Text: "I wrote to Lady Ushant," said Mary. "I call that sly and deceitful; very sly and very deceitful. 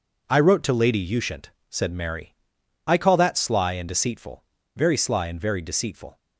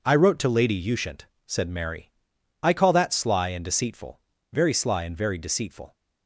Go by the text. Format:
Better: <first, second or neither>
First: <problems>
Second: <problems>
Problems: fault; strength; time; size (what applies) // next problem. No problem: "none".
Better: neither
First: pauses between "Lady" and "Ushant"; slight; at 0.9 s; 0.16 s long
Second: pauses between "Lady" and "Ushant"; slight; at 0.7 s; 0.16 s long